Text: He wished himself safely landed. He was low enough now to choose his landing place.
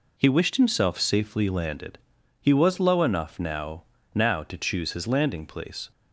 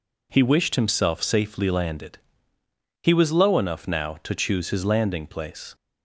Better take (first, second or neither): second